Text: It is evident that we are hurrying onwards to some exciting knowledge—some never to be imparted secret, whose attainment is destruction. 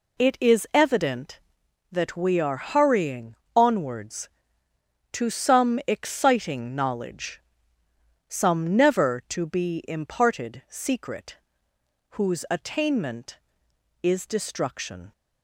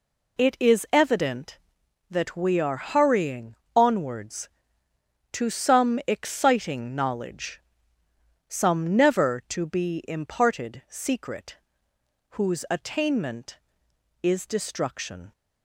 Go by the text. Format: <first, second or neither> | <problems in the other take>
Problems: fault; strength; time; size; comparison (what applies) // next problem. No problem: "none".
neither | pauses between "hurrying" and "onwards"; slight; the same in both